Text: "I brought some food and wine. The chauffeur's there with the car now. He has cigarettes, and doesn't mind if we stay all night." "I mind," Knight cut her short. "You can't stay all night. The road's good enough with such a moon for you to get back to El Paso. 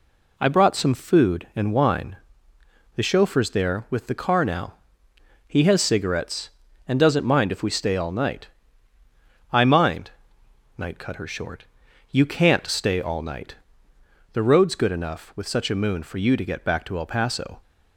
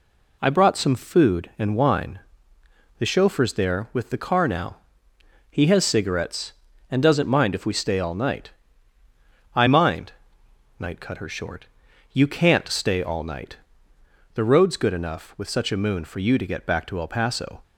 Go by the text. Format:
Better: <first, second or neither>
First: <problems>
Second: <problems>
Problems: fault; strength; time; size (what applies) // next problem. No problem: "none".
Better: neither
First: none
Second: none